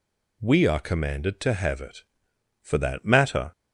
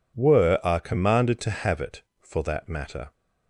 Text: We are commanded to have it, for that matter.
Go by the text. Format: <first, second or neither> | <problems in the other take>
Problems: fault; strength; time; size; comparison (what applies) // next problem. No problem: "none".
first | says "Were" for "We"; at 0.1 s